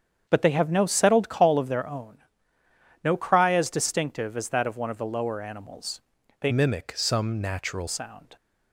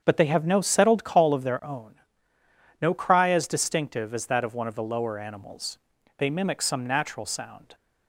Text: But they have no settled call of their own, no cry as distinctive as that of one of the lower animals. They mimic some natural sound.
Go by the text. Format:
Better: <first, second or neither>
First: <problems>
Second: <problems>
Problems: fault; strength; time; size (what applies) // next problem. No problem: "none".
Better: second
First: starts louder than the rest; strong; until 1.3 s; 7.5 dB // changes voice from "mimic" to "natural"; from 6.4 to 7.8 s; 1.4 s long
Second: starts louder than the rest; strong; until 1.0 s; 7.5 dB